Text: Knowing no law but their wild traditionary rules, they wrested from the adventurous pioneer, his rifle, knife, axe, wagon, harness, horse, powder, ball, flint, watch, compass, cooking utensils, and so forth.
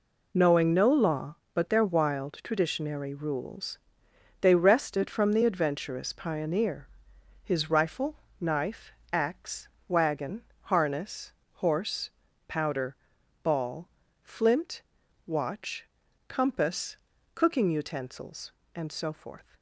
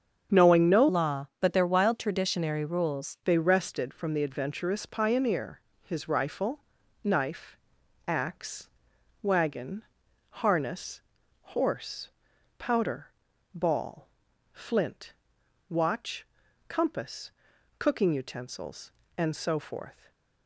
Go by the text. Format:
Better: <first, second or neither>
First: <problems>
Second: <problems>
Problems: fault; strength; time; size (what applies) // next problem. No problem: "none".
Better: first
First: none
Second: starts louder than the rest; strong; until 1.4 s; 7.5 dB // changes voice from "law" to "rules"; from 0.8 to 3.1 s; 2.3 s long